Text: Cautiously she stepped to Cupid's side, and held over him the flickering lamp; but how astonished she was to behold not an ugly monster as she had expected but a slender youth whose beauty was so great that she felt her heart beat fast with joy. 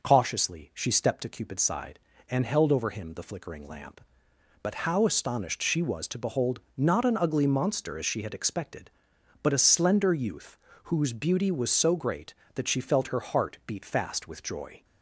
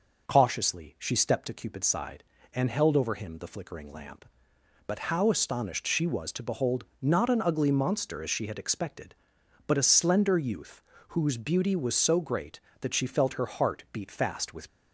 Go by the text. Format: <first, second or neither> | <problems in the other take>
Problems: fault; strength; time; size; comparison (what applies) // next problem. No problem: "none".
first | pauses between "behold" and "not"; slight; at 6.8 s; 0.16 s long; slight in the first // pauses between "youth" and "whose"; slight; at 10.7 s; 0.28 s long; slight in the first // stops before "joy"; at 14.6 s